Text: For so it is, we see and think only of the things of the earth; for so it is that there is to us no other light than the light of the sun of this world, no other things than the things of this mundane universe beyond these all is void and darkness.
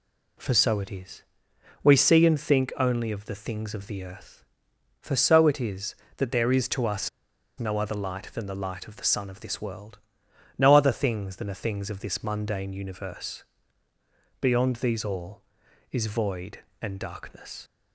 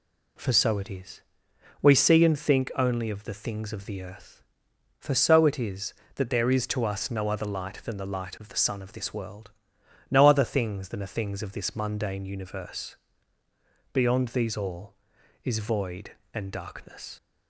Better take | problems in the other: second | pauses between "us" and "no"; noticeable; at 7.0 s; 0.50 s long // pauses between "universe" and "beyond"; noticeable; at 13.4 s; 0.98 s long; noticeable in the second

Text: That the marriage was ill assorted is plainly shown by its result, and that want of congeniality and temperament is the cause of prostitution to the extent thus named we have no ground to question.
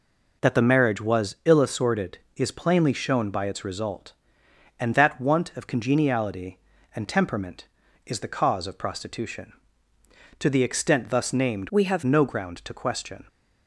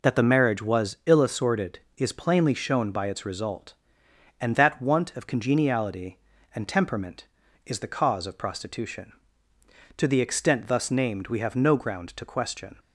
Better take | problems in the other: second | changes voice from "we" to "have"; from 11.6 to 12.0 s; 0.4 s long

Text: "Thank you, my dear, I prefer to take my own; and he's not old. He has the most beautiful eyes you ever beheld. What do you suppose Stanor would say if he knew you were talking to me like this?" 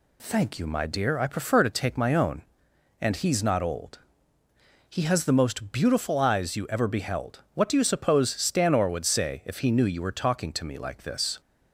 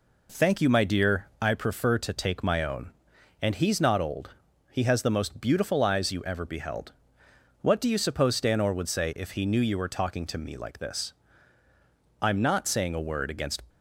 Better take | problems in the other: first | goes on to say "I'm not saying a word against"; from 12.1 s on; 1.4 s long

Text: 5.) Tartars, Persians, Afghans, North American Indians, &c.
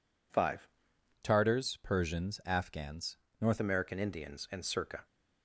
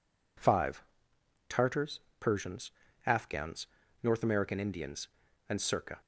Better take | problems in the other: second | changes voice from "Tartars" to "North"; from 1.2 to 3.5 s; 2.3 s long

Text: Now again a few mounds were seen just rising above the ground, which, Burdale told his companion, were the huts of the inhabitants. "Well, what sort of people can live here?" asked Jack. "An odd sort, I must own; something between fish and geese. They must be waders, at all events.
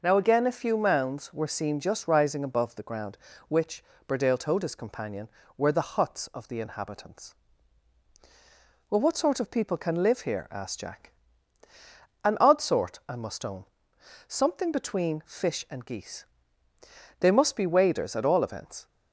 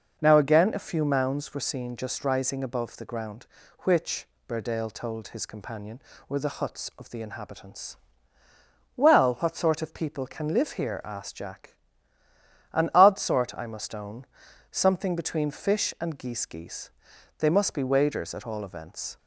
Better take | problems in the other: first | says "geese" twice; at 16.4 s

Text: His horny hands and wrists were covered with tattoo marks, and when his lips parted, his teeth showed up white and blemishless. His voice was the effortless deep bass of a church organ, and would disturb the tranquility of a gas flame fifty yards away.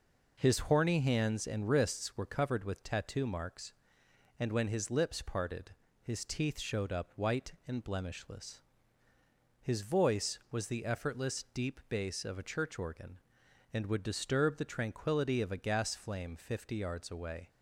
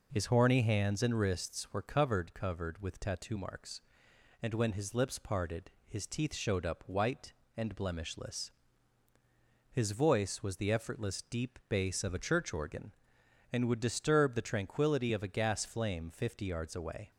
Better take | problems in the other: first | says "covered" twice; at 2.3 s

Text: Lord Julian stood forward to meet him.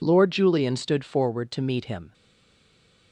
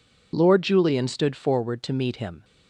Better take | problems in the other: second | stays silent after the last word; from 2.1 s on; 1.0 s long

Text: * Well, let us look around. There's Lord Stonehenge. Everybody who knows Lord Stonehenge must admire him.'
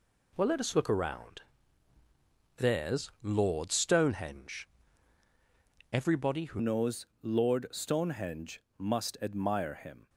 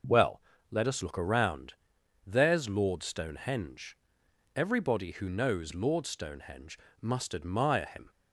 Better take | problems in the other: second | changes voice at "knows"; from 6.6 s on; 3.4 s long // pauses between "knows" and "Lord"; slight; at 7.0 s; 0.16 s long // pauses between "Stonehenge" and "must"; slight; at 8.6 s; 0.16 s long; slight in the second

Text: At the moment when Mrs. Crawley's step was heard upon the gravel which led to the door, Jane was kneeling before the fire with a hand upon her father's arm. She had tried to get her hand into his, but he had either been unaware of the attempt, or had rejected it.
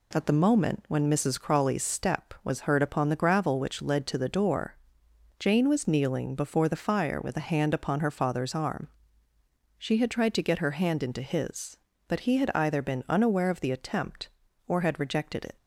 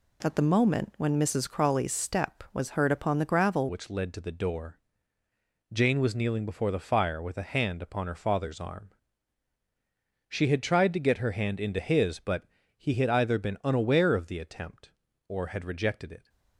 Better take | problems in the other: first | changes voice at "which"; from 3.6 s on; 12.6 s long // pauses between "but" and "he"; slight; at 12.4 s; 0.32 s long

